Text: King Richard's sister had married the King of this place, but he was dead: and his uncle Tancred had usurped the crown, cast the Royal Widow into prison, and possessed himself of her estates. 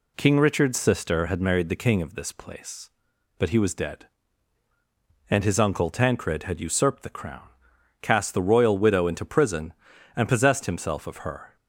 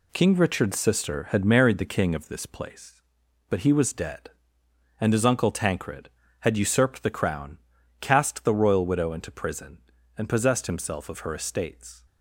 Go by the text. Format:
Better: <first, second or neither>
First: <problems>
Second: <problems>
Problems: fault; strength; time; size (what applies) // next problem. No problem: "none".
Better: second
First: stops before "estates"; at 11.5 s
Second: none